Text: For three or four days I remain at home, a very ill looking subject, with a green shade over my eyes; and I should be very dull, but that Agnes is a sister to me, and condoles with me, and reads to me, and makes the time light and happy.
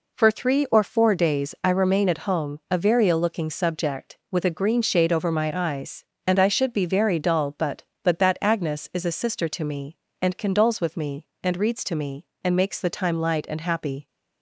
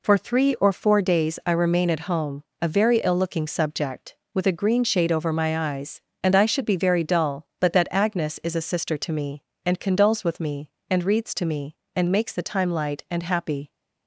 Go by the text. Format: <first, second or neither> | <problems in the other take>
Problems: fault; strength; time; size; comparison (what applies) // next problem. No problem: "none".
second | says "but" twice; at 8.0 s